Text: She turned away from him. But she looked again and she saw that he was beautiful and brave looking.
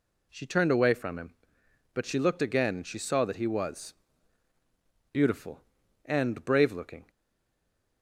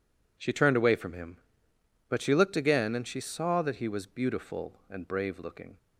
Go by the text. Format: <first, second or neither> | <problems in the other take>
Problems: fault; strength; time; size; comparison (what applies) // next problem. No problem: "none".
second | pauses between "was" and "beautiful"; at 3.9 s; 1.1 s long // stays silent after the last word; slight; from 7.1 s on; 0.9 s long